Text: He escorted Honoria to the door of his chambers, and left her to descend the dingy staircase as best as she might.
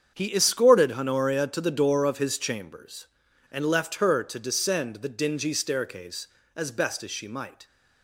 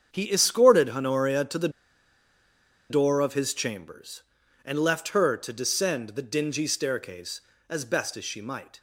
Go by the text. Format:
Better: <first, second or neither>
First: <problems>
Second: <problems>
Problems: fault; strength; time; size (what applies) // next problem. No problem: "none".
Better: first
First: starts louder than the rest; strong; until 1.1 s; 7.5 dB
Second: starts louder than the rest; strong; until 1.1 s; 7.5 dB // pauses between "the" and "door"; at 1.6 s; 1.2 s long